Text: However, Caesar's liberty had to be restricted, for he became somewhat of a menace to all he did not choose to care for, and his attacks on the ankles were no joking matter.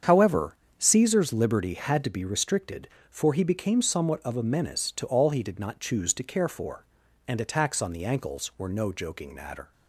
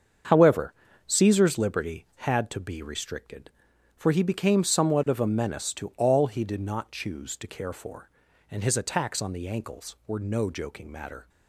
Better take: second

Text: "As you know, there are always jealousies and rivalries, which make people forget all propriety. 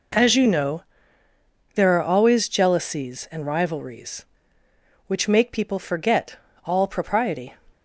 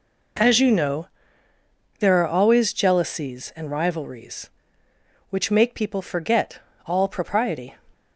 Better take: neither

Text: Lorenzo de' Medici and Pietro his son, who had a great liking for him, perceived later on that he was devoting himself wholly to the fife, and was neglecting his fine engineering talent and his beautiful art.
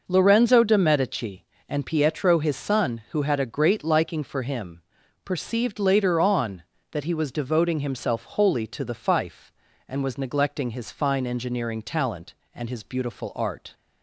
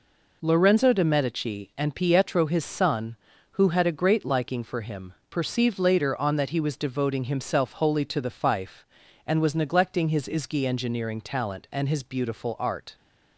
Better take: first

